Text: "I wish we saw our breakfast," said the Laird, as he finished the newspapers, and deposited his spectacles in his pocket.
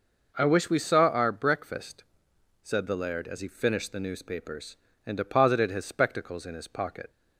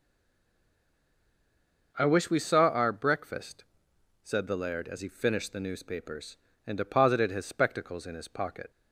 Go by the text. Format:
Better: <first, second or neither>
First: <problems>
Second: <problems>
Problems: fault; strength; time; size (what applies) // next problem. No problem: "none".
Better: first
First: none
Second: stays silent before the first word; noticeable; until 1.9 s; 1.9 s long